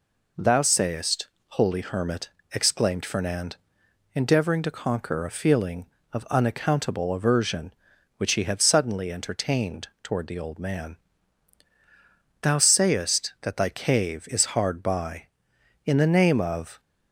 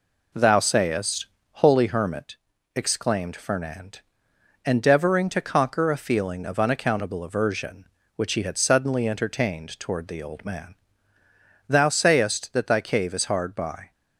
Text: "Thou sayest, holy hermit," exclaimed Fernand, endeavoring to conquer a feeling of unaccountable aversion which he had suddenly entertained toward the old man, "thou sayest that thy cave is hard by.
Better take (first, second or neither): second